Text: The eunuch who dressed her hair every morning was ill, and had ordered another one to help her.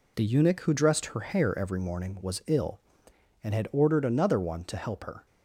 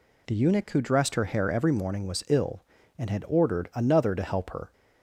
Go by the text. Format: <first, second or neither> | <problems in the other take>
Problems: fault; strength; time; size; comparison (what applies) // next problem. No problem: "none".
first | skips "one"; at 4.1 s